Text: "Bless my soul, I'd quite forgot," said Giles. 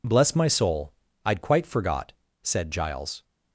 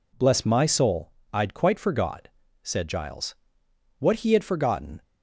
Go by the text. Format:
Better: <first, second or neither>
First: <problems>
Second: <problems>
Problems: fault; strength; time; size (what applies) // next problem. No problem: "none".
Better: first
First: none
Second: goes on to say "What he had forgotten"; noticeable; from 3.9 s on; 1.0 s long